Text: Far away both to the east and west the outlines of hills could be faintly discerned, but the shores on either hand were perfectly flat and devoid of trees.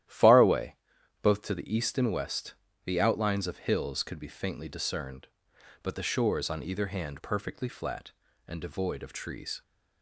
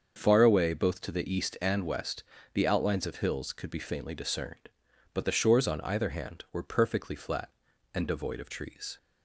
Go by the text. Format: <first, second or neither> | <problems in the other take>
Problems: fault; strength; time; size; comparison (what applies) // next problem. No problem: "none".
second | starts louder than the rest; strong; until 1.5 s; 12 dB; also in the second // pauses between "away" and "both"; noticeable; at 0.7 s; 0.46 s long // pauses between "west" and "the"; slight; at 2.5 s; 0.32 s long; slight in the second // skips "were"; at 7.1 s